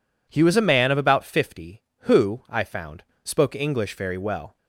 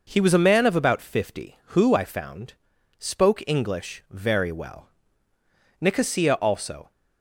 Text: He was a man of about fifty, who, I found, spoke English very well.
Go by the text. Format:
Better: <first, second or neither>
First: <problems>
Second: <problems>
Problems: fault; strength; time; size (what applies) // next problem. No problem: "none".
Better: first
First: none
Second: goes on to say "Nicosia also"; noticeable; from 5.8 s on; 1.1 s long